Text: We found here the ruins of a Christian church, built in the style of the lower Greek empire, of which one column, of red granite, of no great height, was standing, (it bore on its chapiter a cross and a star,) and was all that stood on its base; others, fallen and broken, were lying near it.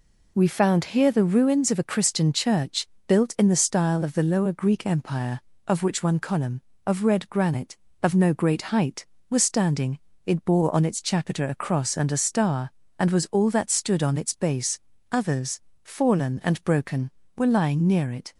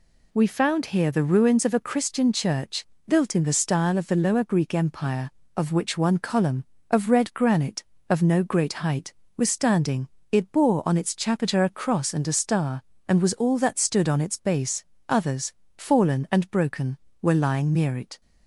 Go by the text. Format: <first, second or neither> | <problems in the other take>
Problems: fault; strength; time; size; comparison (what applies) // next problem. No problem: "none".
neither | none